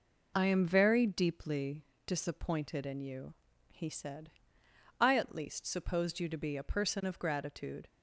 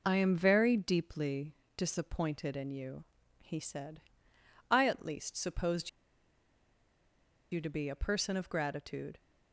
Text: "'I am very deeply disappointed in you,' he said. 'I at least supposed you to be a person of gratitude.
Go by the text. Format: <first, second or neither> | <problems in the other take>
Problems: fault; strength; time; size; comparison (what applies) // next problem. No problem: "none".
first | pauses between "deeply" and "disappointed"; slight; at 1.5 s; 0.24 s long; slight in the first // pauses between "supposed" and "you"; strong; at 5.8 s; 1.6 s long